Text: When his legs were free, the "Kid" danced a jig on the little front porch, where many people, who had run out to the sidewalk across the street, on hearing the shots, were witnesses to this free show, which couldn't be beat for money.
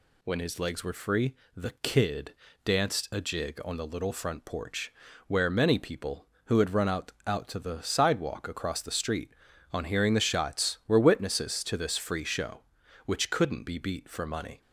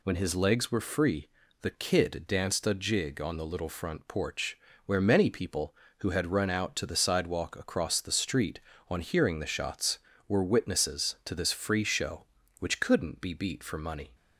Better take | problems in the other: second | pauses between "Kid" and "danced"; slight; at 2.3 s; 0.28 s long // says "out" twice; at 7.2 s

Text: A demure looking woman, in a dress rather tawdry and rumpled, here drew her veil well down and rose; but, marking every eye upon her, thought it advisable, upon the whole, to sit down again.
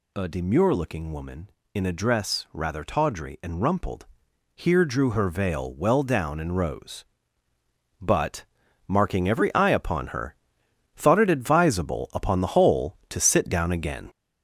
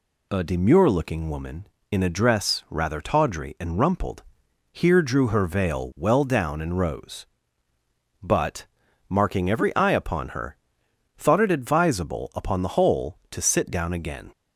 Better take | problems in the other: second | gets louder; noticeable; throughout; 5.5 dB

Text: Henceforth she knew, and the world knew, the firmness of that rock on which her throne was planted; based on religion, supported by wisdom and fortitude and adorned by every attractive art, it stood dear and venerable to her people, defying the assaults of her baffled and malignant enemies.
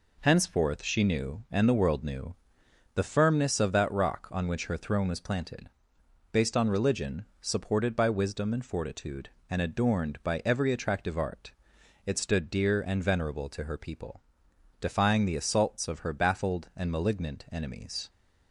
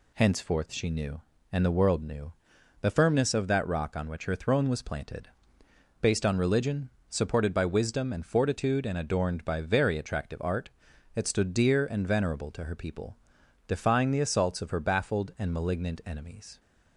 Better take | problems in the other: first | says "very" for "every"; at 9.5 s

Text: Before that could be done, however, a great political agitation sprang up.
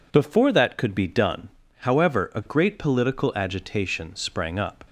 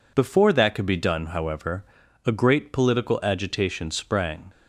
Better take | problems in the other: first | stops before "up"; at 4.5 s

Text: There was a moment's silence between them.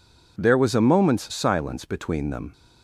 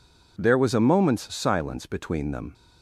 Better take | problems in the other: neither | none

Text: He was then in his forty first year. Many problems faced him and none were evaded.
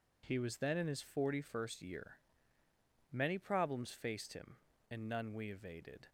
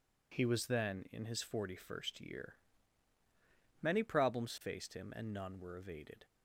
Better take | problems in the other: second | says "we" for "were"; at 5.3 s

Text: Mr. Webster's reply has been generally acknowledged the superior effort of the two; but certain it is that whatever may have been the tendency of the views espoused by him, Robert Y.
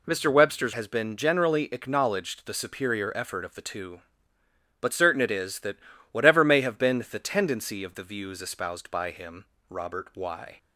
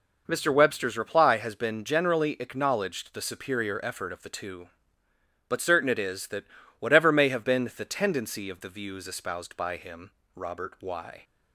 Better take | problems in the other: second | skips "reply"; at 0.7 s // pauses between "that" and "whatever"; slight; at 5.7 s; 0.34 s long; slight in the second

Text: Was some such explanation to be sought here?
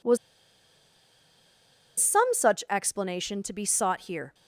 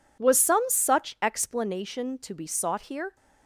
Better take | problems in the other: second | pauses between "Was" and "some"; strong; at 0.1 s; 1.8 s long

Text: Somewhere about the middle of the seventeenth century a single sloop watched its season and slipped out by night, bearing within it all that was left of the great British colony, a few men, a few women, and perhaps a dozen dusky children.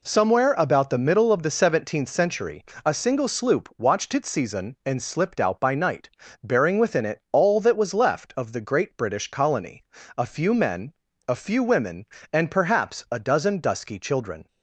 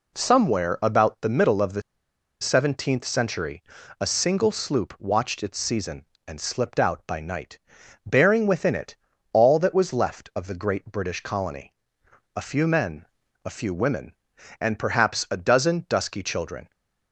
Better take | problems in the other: first | pauses between "the" and "seventeenth"; noticeable; at 1.8 s; 0.59 s long // pauses between "century" and "a"; at 3.6 s; 0.38 s long; slight in the first // pauses between "it" and "all"; at 8.9 s; 0.38 s long

